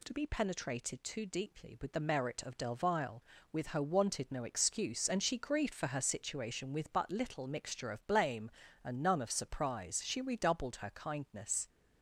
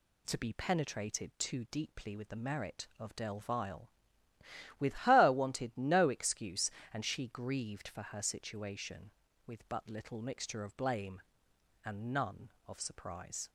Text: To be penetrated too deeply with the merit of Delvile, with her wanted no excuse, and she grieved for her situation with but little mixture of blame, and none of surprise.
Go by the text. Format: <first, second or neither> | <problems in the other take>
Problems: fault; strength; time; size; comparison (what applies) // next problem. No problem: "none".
second | goes on to say "She redoubled her kindness"; from 10.0 s on; 1.6 s long